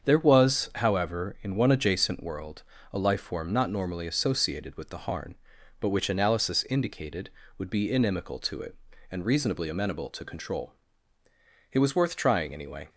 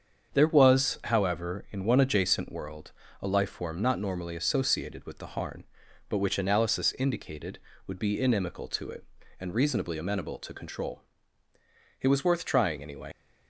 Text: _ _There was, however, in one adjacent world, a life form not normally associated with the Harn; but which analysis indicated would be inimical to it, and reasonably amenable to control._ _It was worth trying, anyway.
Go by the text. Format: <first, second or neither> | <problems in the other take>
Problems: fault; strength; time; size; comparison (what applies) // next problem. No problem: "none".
first | starts louder than the rest; strong; until 1.4 s; 7 dB; strong in the first // leaves "anyway" unfinished; at 13.1 s; 60 ms